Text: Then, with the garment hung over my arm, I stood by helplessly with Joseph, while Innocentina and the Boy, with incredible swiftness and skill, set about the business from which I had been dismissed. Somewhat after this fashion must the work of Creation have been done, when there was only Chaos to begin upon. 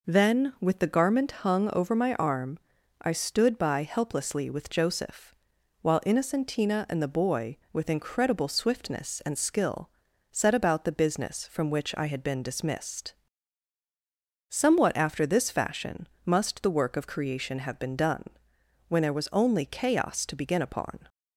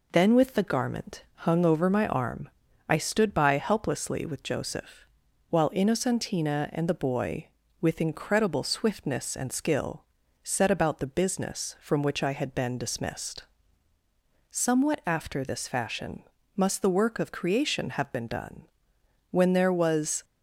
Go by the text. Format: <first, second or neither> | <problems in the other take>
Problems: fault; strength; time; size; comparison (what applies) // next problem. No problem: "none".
first | pauses between "garment" and "hung"; slight; at 1.2 s; 0.18 s long // pauses between "fashion" and "must"; slight; at 16.2 s; 0.32 s long; slight in the first // stops before "only Chaos to begin upon"; at 20.2 s